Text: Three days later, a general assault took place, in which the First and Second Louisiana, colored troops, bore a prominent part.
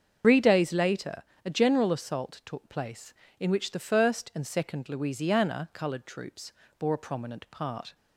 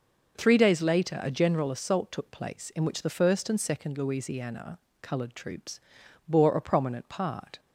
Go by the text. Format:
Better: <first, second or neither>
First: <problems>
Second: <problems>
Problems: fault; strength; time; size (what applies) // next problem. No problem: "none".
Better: second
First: loses the start of "Three"; at 0.2 s; 80 ms // starts louder than the rest; until 1.4 s; 7 dB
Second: none